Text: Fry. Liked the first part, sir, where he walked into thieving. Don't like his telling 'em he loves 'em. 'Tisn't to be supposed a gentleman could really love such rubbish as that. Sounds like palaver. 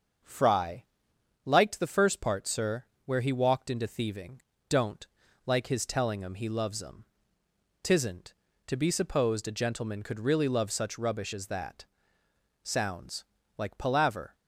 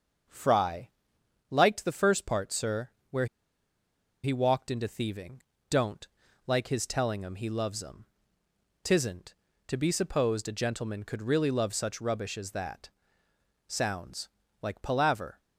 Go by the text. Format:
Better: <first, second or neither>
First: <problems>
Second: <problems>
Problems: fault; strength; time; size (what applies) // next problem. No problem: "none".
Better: first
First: starts louder than the rest; until 1.8 s; 6.5 dB // pauses between "Don't" and "like"; at 5.0 s; 0.38 s long // pauses between "Sounds" and "like"; slight; at 13.2 s; 0.34 s long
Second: starts louder than the rest; until 1.9 s; 6.5 dB // pauses between "where" and "he"; noticeable; at 3.2 s; 0.97 s long // pauses between "Don't" and "like"; at 6.0 s; 0.38 s long // pauses between "Sounds" and "like"; slight; at 14.2 s; 0.34 s long